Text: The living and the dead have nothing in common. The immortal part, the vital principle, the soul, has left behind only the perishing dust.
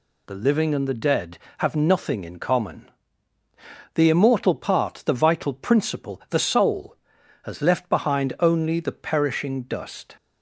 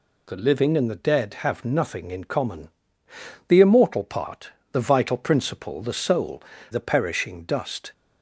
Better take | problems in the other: first | skips "has left behind only"; at 6.5 s

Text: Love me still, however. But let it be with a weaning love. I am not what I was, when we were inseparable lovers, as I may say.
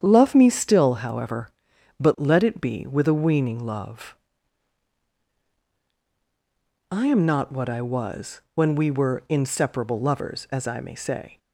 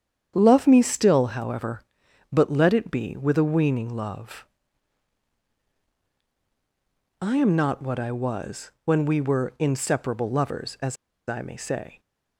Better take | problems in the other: first | starts louder than the rest; strong; until 1.3 s; 8.5 dB; strong in the first // pauses between "as" and "I"; slight; at 10.9 s; 0.31 s long

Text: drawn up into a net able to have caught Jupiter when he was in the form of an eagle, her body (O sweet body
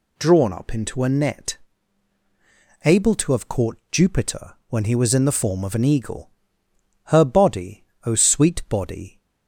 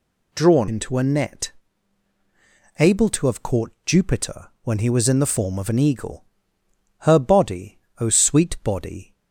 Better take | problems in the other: first | skips "up"; at 0.6 s // pauses between "net" and "able"; strong; at 1.5 s; 1.2 s long; strong in the first // pauses between "caught" and "Jupiter"; slight; at 3.7 s; 0.16 s long; slight in the first

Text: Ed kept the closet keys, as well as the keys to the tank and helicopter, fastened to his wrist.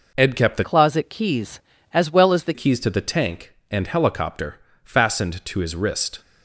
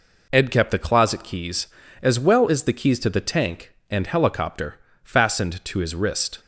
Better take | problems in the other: second | changes voice from "closet" to "the"; from 0.6 to 2.5 s; 1.9 s long

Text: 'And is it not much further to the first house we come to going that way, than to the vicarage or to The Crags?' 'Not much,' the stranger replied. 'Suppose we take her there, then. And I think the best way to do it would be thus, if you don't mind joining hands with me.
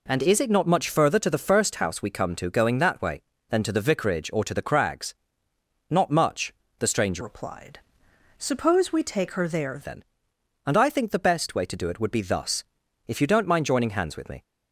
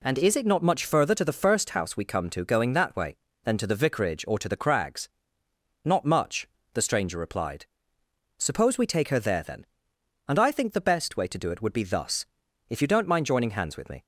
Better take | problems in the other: second | changes voice from "replied" to "there"; from 7.2 to 9.7 s; 2.5 s long

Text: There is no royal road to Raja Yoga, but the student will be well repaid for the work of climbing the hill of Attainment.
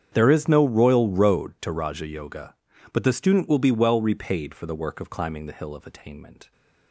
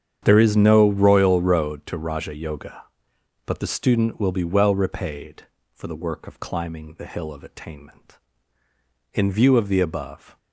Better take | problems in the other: first | starts louder than the rest; strong; until 1.2 s; 8.5 dB; strong in the first // goes on to say "In view of the above"; noticeable; from 9.1 s on; 1.2 s long

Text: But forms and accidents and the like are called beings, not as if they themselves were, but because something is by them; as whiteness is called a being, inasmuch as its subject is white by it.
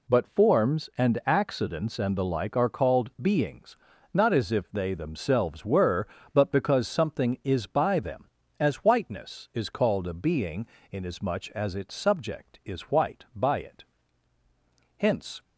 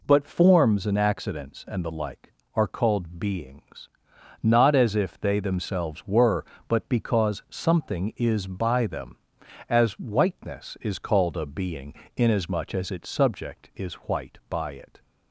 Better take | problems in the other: second | goes on to say "Hence"; slight; from 14.9 s on; 0.46 s long

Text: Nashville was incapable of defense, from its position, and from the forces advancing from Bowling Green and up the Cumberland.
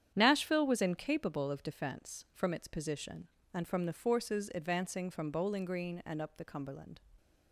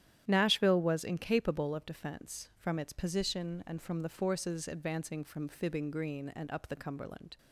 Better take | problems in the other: first | starts louder than the rest; strong; until 1.2 s; 11 dB; strong in the first // says "Fibbing" for "Bowling"; at 5.4 s

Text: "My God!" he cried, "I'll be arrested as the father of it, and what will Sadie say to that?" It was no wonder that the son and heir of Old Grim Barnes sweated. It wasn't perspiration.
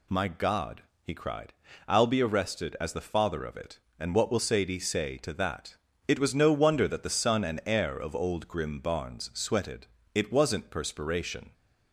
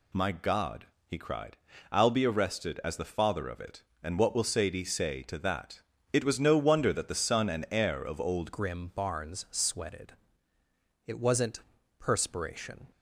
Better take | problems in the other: first | changes voice at "Grim"; from 8.5 s on; 4.3 s long // pauses between "wasn't" and "perspiration"; at 11.6 s; 0.38 s long

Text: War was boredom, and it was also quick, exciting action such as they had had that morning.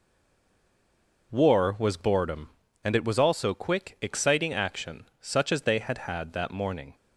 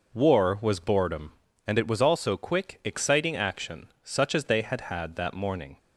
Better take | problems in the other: second | stays silent before the first word; noticeable; until 1.3 s; 1.3 s long // pauses between "action" and "such"; slight; at 5.0 s; 0.16 s long; slight in the second

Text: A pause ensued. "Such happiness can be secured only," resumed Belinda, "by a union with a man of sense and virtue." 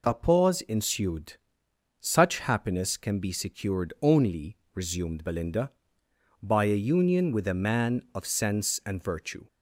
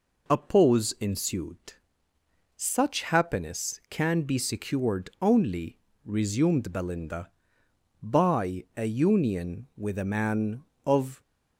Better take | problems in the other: first | stops before "sense and virtue"; at 11.2 s

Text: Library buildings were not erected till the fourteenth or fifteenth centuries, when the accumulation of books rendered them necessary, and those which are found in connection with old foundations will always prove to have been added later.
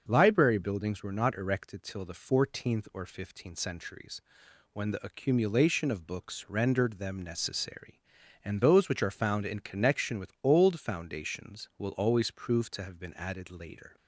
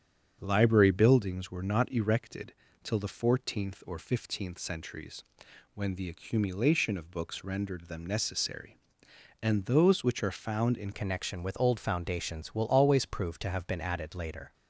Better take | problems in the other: first | starts louder than the rest; strong; until 1.4 s; 8 dB; also in the first // pauses between "erected" and "till"; slight; at 2.5 s; 0.28 s long // changes voice at "connection"; from 10.9 s on; 3.6 s long

